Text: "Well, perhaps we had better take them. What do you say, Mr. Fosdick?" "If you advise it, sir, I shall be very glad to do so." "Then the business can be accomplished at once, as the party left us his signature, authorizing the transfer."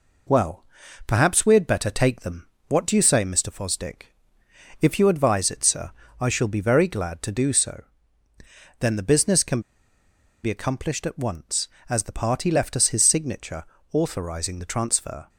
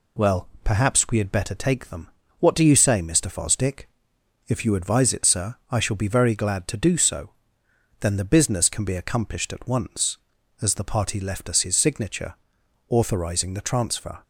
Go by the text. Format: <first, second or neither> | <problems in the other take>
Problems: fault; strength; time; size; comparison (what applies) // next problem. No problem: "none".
second | pauses between "can" and "be"; noticeable; at 9.6 s; 0.81 s long